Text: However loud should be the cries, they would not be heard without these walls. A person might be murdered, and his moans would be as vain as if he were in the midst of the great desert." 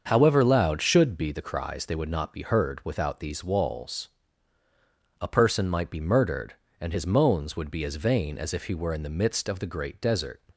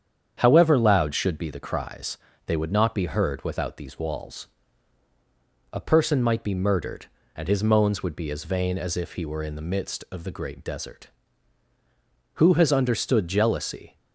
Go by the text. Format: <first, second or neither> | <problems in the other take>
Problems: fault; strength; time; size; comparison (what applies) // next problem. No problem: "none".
first | starts louder than the rest; strong; until 1.3 s; 8 dB; also in the first // goes on to say "Who has understood jealousy"; from 12.3 s on; 1.6 s long